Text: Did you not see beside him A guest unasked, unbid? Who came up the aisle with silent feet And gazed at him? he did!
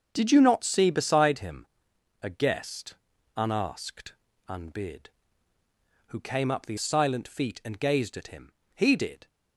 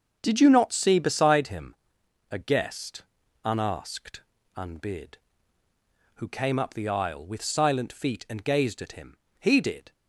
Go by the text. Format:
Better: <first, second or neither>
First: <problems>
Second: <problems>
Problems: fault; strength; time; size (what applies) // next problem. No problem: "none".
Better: second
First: starts louder than the rest; until 1.1 s; 6 dB // pauses between "him" and "A"; noticeable; at 1.6 s; 0.54 s long // pauses between "guest" and "unasked"; at 2.9 s; 0.40 s long // skips "aisle with"; at 6.7 s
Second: starts louder than the rest; until 1.2 s; 6.5 dB // pauses between "him" and "A"; noticeable; at 1.7 s; 0.54 s long // pauses between "guest" and "unasked"; at 3.0 s; 0.40 s long